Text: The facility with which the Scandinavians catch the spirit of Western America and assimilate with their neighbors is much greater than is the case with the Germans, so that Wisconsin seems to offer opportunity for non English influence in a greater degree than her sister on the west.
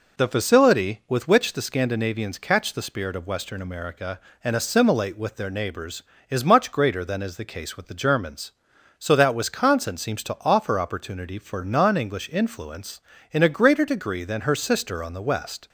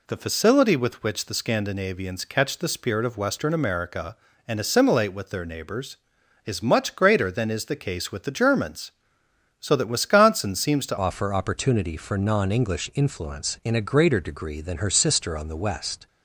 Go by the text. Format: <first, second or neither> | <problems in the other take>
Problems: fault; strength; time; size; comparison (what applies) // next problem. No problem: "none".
first | changes voice at "offer"; from 10.9 s on; 5.1 s long